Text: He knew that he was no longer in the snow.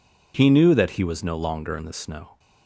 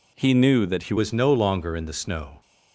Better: first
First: none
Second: changes voice at "was"; from 0.9 s on; 1.5 s long

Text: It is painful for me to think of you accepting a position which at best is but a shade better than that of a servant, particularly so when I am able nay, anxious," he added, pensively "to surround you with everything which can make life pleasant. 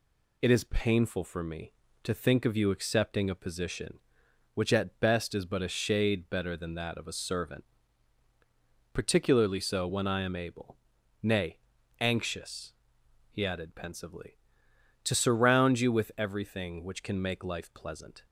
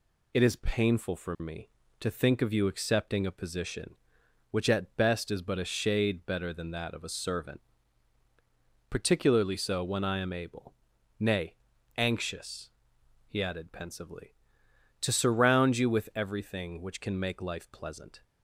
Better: neither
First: pauses between "able" and "nay"; noticeable; at 10.7 s; 0.46 s long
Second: pauses between "able" and "nay"; noticeable; at 10.7 s; 0.46 s long

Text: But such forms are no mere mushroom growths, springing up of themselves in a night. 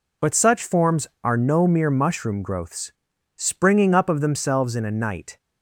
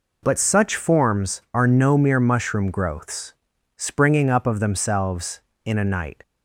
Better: neither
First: none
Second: none

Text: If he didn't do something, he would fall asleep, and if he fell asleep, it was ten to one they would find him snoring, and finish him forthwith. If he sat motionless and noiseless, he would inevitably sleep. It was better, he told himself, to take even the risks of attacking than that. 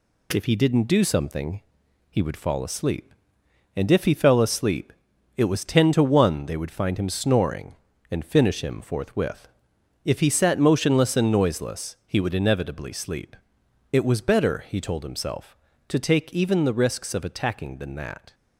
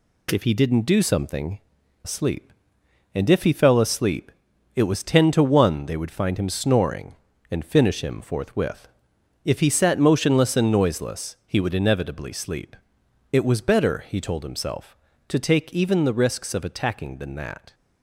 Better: first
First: none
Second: skips "he would fall"; at 1.8 s

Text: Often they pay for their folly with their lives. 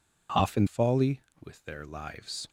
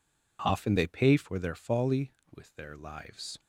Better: second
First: skips "they pay for their"; at 0.6 s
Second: none

